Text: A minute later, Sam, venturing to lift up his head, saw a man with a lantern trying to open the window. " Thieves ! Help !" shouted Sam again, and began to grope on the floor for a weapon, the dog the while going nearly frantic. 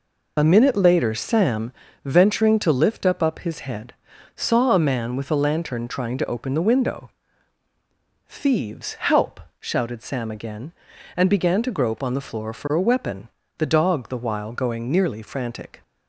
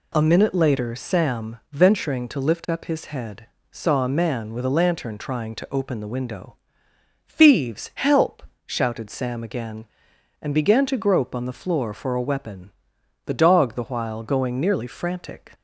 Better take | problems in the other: second | says "up" twice; at 3.2 s

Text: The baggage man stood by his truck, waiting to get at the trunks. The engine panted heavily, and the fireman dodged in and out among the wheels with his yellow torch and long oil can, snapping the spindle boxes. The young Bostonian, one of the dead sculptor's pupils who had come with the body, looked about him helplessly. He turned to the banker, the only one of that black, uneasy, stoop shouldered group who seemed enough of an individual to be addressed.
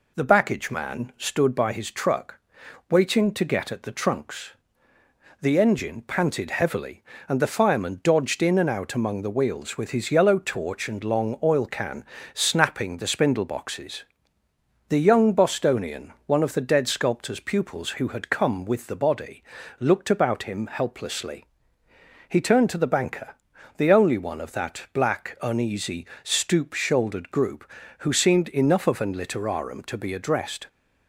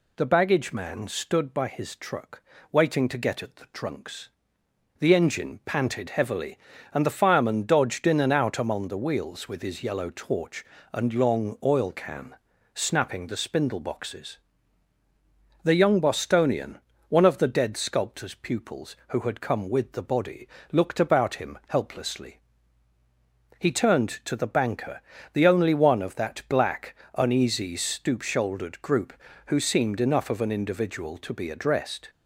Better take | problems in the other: second | says "literarum" for "individual"; at 29.1 s

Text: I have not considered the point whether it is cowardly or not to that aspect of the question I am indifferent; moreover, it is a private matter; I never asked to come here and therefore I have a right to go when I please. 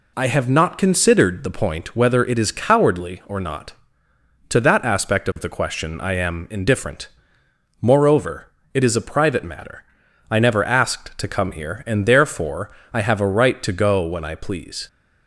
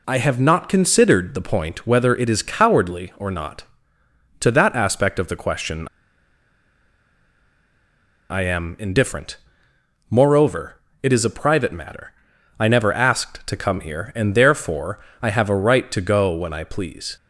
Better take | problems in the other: first | pauses between "question" and "I"; strong; at 5.8 s; 2.4 s long // pauses between "therefore" and "I"; slight; at 14.9 s; 0.22 s long; slight in the first

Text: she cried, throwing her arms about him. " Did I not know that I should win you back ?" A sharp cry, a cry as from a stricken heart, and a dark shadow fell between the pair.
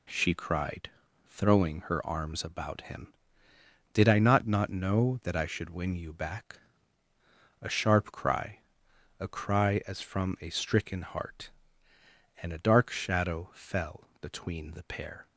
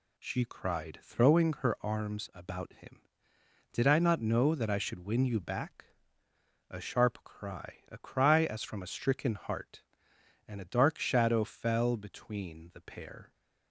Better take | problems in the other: second | says "not" twice; at 4.4 s

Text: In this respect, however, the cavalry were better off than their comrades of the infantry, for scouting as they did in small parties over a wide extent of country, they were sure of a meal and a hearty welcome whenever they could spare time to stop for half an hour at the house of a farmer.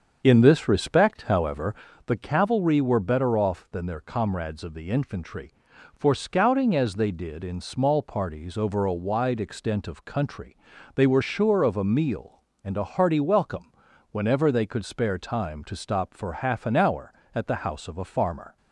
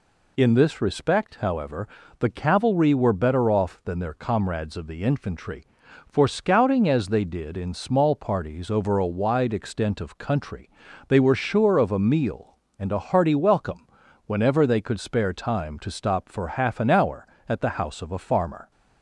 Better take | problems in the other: second | starts louder than the rest; until 1.9 s; 7 dB // pauses between "welcome" and "whenever"; at 13.7 s; 0.40 s long; also in the second

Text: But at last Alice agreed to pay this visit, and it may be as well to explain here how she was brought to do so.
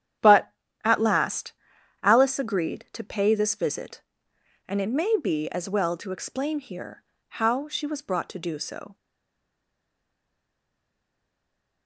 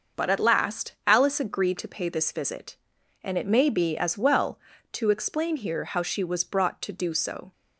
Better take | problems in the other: second | starts louder than the rest; strong; until 2.0 s; 9.5 dB; also in the second // pauses between "last" and "Alice"; noticeable; at 1.5 s; 0.50 s long // pauses between "here" and "how"; slight; at 7.0 s; 0.26 s long // stays silent after the last word; strong; from 8.9 s on; 2.9 s long

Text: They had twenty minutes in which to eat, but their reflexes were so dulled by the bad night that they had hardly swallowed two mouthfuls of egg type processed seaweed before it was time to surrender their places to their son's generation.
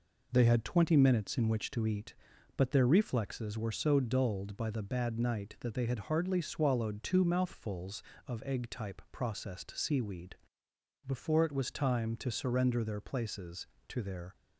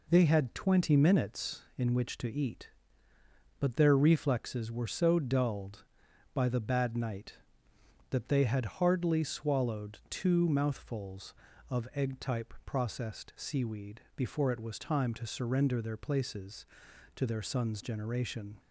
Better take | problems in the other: second | pauses between "seaweed" and "before"; noticeable; at 10.3 s; 0.72 s long; slight in the second // stops before "son's generation"; at 14.3 s

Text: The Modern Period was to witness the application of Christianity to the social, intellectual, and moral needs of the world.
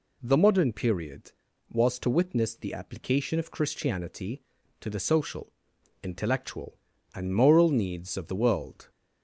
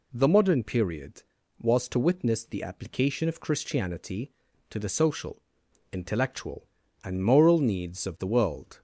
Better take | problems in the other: neither | none

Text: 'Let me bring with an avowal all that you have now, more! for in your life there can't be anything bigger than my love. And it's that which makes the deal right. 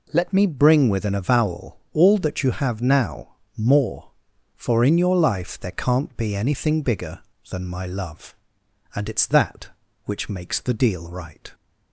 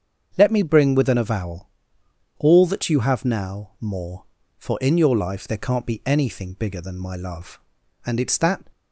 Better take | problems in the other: first | starts louder than the rest; strong; until 1.3 s; 7 dB // pauses between "avowal" and "all"; noticeable; at 1.6 s; 0.70 s long // stops before "which makes the deal right"; at 8.7 s

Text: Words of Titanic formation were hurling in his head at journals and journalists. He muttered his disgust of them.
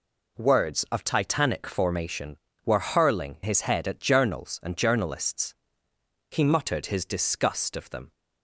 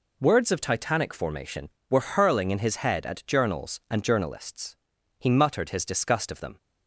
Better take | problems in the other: second | skips "in"; at 3.3 s

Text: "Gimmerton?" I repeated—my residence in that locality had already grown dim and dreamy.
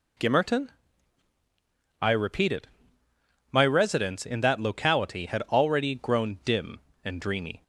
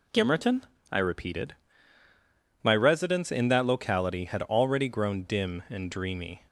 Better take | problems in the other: neither | none

